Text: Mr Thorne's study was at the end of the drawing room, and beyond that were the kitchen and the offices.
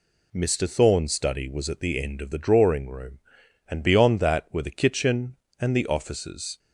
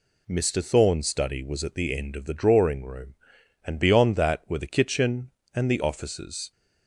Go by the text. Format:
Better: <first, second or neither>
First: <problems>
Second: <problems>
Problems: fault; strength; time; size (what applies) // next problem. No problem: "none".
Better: neither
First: none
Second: none